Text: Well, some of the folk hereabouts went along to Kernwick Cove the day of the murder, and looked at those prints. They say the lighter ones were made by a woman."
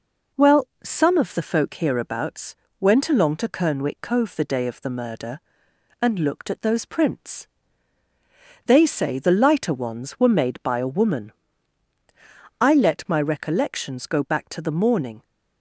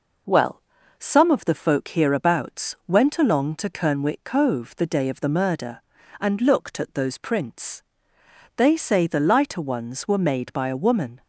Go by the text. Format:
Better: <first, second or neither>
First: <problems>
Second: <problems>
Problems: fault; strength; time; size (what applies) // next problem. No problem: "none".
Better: second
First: pauses between "hereabouts" and "went"; slight; at 2.5 s; 0.26 s long // goes on to say "I let my recollections go back to the morning"; strong; from 12.6 s on; 2.6 s long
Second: none